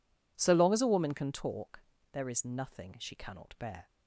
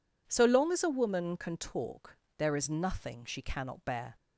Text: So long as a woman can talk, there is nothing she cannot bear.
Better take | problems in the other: neither | none

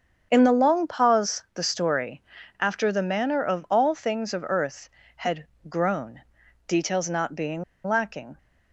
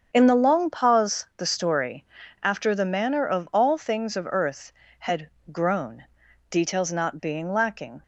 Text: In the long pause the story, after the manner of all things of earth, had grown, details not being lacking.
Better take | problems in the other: second | starts louder than the rest; strong; until 1.3 s; 7 dB; strong in the second // pauses between "had" and "grown"; slight; at 5.4 s; 0.24 s long; slight in the second // pauses between "being" and "lacking"; slight; at 7.6 s; 0.23 s long

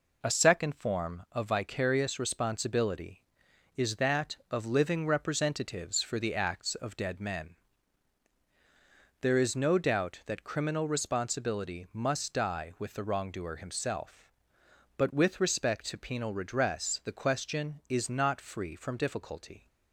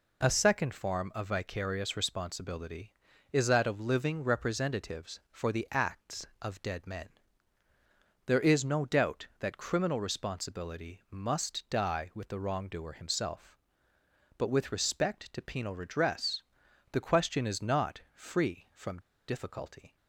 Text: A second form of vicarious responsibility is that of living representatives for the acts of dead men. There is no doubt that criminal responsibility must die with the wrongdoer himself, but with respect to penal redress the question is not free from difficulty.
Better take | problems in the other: first | pauses between "redress" and "the"; noticeable; at 16.4 s; 0.48 s long // pauses between "from" and "difficulty"; slight; at 18.9 s; 0.28 s long

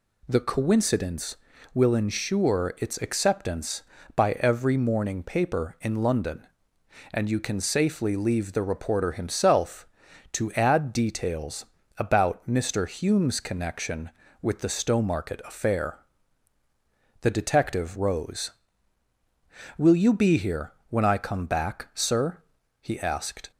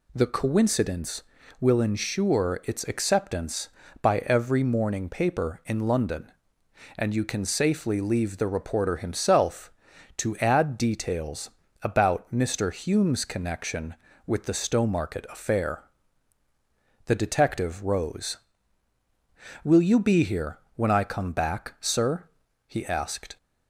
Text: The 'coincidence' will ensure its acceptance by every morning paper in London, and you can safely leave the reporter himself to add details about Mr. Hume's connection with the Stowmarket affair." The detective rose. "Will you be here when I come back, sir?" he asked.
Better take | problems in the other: neither | pauses between "details" and "about"; slight; the same in both // pauses between "here" and "when"; slight; the same in both

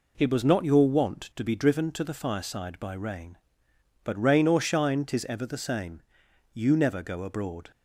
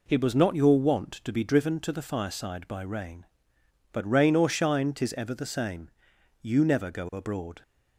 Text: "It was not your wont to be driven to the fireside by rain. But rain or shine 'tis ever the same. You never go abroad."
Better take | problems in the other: neither | none

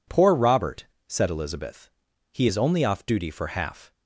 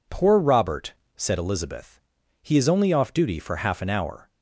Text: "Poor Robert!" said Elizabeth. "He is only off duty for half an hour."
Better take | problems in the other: second | stops before "an hour"; at 3.9 s

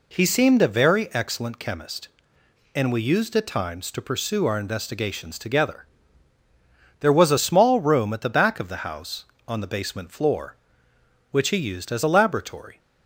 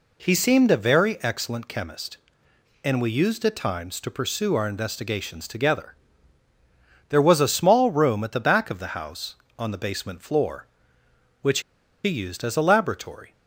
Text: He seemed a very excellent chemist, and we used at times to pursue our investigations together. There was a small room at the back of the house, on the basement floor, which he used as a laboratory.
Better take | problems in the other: first | pauses between "which" and "he"; at 11.6 s; 0.43 s long

